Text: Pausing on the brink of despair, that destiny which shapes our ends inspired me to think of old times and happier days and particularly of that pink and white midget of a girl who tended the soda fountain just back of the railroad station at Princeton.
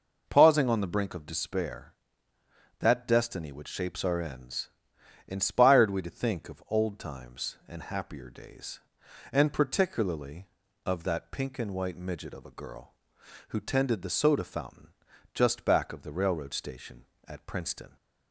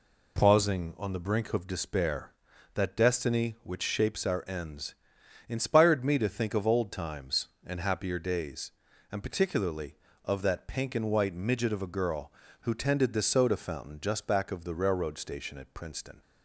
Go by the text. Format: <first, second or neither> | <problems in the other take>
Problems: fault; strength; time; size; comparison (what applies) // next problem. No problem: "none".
second | pauses between "ends" and "inspired"; noticeable; at 4.6 s; 0.58 s long; noticeable in the second // says "we" for "me"; at 5.8 s // pauses between "fountain" and "just"; at 14.8 s; 0.44 s long